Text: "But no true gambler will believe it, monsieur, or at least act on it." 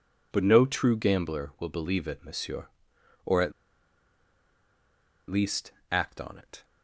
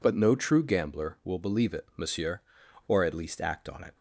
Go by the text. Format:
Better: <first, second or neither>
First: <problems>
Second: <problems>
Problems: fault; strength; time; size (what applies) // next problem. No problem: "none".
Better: second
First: pauses between "at" and "least"; strong; at 3.5 s; 1.7 s long // pauses between "least" and "act"; slight; at 5.7 s; 0.22 s long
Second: none